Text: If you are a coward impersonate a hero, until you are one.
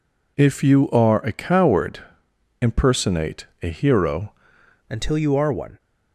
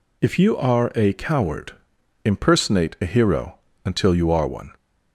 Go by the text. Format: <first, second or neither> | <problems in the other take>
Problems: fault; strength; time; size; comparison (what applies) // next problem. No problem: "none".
second | pauses between "coward" and "impersonate"; noticeable; at 1.9 s; 0.64 s long; noticeable in the second // pauses between "impersonate" and "a"; slight; at 3.4 s; 0.16 s long // changes voice at "until"; from 4.8 s on; 0.9 s long